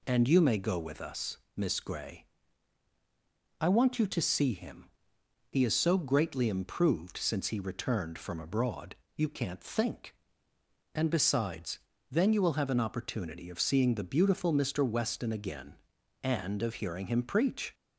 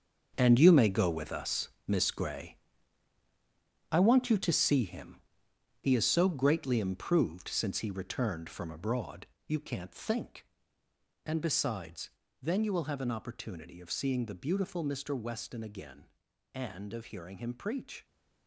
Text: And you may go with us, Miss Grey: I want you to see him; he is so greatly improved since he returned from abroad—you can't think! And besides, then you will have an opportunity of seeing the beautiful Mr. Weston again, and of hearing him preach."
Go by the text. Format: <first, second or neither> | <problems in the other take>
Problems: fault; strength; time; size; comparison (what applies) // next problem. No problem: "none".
first | gets quieter; strong; throughout; 11.5 dB